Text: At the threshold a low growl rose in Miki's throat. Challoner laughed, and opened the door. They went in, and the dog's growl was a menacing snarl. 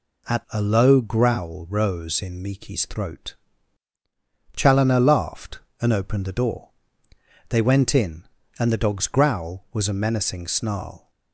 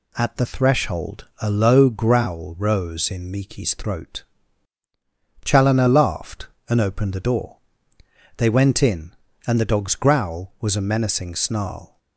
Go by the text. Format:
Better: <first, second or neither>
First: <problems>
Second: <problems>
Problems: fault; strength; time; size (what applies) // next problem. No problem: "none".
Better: second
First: skips "the threshold"; at 0.4 s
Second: none